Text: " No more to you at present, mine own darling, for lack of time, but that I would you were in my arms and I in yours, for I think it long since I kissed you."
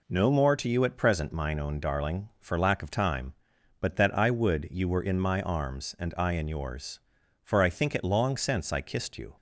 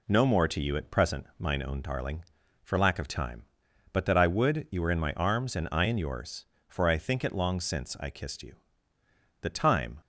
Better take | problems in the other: first | goes on to say "The time"; from 9.4 s on; 0.60 s long

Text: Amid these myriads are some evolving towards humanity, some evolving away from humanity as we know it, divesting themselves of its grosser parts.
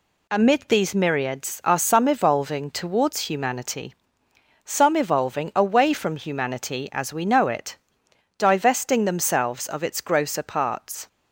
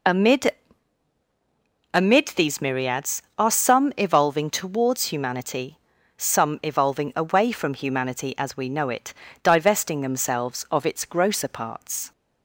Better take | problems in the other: first | says "Amid" twice; at 1.9 s

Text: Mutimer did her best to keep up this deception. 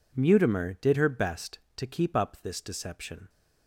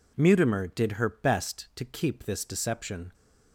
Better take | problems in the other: first | skips "up"; at 2.2 s

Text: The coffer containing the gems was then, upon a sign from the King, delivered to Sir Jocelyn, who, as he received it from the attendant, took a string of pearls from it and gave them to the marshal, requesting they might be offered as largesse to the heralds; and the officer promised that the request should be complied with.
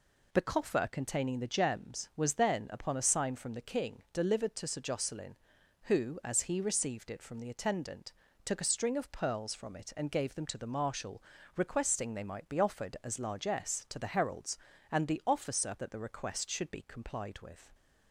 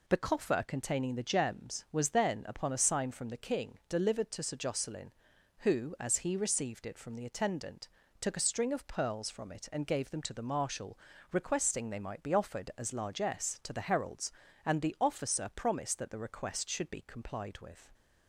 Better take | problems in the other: second | skips "promised"; at 15.7 s

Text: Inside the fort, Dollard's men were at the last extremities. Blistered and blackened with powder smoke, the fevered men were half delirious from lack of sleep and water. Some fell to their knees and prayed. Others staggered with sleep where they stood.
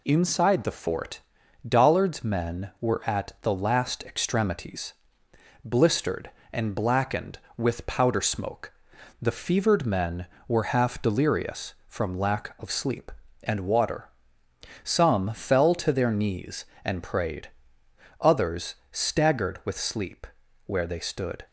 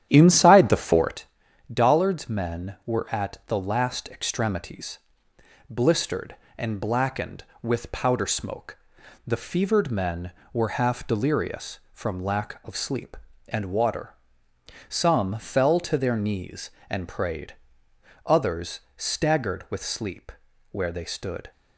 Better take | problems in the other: first | starts louder than the rest; strong; until 1.2 s; 10.5 dB // pauses between "Others" and "staggered"; slight; at 18.7 s; 0.18 s long; slight in the first // pauses between "sleep" and "where"; at 20.3 s; 0.40 s long; also in the first

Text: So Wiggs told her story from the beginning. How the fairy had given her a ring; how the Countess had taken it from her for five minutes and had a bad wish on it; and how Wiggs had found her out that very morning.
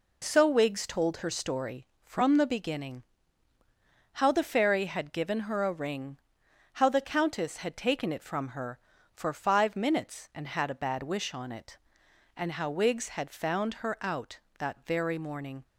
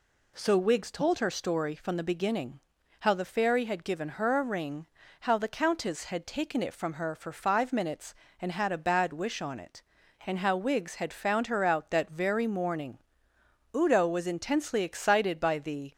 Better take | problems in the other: first | goes on to say "Udo was intensely excited by the"; strong; from 13.7 s on; 2.1 s long

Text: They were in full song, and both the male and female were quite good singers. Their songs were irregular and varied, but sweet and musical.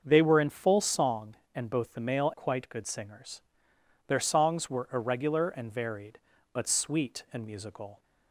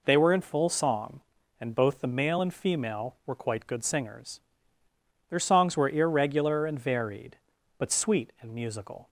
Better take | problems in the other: second | starts louder than the rest; until 1.0 s; 6.5 dB // skips "and female were"; at 2.3 s

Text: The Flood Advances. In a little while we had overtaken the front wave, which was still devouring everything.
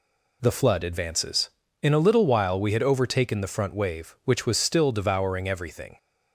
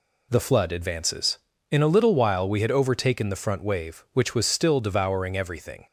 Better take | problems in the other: neither | none

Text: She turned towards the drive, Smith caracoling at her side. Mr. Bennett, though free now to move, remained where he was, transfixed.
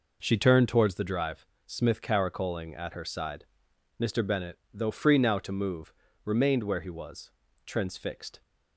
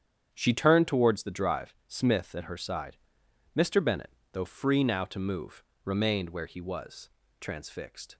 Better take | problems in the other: first | starts louder than the rest; strong; until 1.3 s; 9 dB // skips "caracoling"; at 2.3 s

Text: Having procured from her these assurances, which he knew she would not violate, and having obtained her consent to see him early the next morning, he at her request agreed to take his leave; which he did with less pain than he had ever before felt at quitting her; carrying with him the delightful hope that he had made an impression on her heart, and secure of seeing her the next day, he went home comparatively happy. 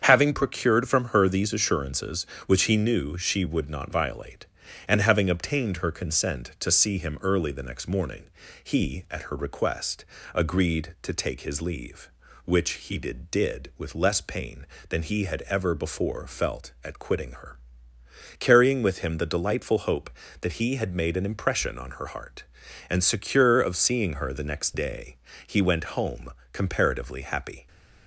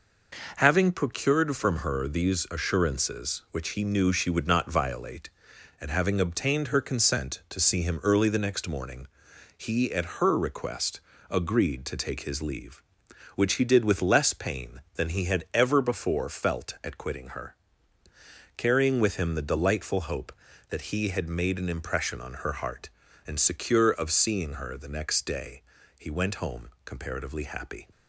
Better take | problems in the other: second | starts louder than the rest; strong; until 1.0 s; 7.5 dB // pauses between "request" and "agreed"; slight; at 10.0 s; 0.28 s long; slight in the second // says "did" twice; at 13.2 s // pauses between "home" and "comparatively"; slight; at 26.3 s; 0.22 s long; slight in the second

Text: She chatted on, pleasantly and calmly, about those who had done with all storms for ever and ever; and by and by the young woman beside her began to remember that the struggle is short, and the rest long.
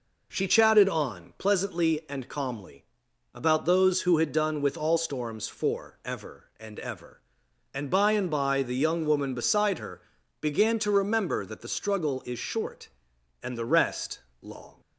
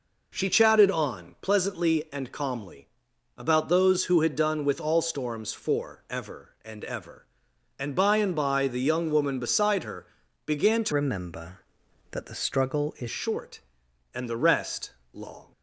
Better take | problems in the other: first | pauses between "her" and "began"; at 10.0 s; 0.40 s long; also in the first // changes voice from "remember" to "is"; from 10.9 to 13.0 s; 2.1 s long // pauses between "rest" and "long"; slight; at 14.8 s; 0.24 s long; slight in the first

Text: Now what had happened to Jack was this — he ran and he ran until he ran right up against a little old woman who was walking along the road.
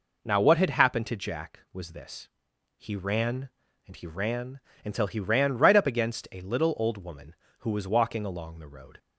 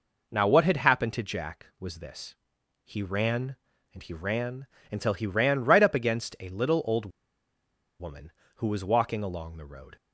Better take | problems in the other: first | pauses between "ran" and "until"; slight; at 4.6 s; 0.26 s long; slight in the first // pauses between "old" and "woman"; noticeable; at 7.0 s; 0.90 s long

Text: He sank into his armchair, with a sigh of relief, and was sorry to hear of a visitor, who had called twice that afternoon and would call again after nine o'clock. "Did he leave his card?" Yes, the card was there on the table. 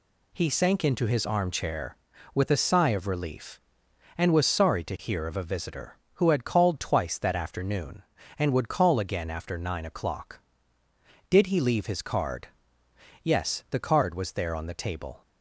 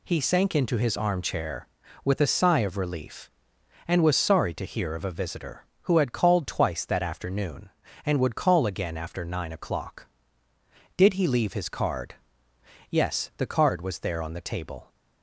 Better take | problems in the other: neither | none

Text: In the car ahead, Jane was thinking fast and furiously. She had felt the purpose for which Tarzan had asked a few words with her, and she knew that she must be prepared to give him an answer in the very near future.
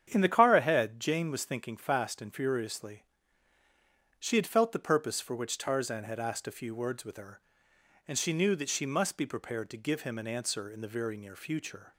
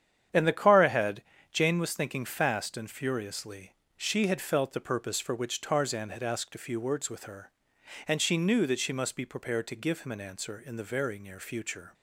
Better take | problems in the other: neither | starts louder than the rest; strong; the same in both

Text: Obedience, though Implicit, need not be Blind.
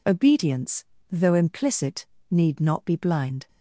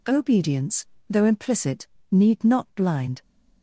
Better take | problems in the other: first | skips "be"; at 2.6 s

